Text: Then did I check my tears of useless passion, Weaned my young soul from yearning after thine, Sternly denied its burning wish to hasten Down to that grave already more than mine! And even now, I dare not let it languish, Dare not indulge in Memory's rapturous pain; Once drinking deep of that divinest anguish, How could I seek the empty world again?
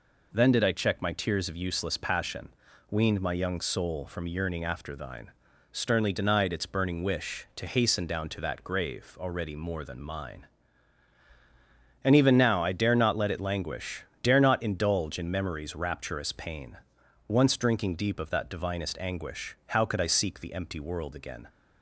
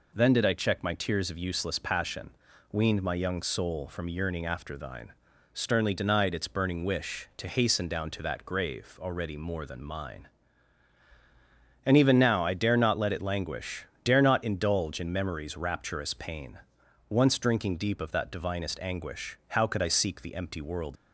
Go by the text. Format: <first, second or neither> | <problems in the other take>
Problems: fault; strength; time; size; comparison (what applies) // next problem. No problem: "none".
first | stops before "again"; at 20.9 s